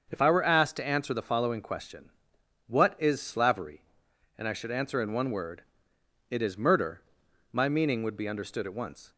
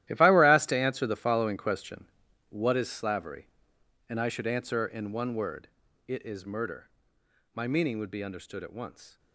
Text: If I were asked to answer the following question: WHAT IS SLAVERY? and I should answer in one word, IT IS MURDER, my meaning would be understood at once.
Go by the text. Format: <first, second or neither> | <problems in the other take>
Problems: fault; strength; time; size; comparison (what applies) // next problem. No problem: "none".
first | gets quieter; strong; throughout; 13.5 dB // starts louder than the rest; strong; until 1.1 s; 13.5 dB; also in the first